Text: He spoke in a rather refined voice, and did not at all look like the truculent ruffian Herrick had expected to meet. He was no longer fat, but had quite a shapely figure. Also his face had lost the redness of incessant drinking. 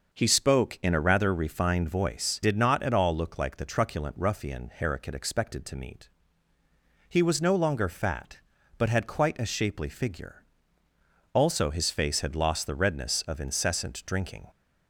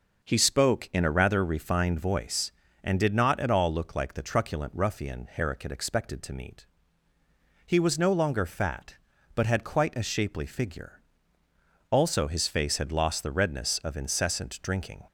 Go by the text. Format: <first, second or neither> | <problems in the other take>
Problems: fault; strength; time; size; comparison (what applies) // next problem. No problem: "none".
second | starts louder than the rest; noticeable; until 1.1 s; 6 dB // skips "and"; at 2.4 s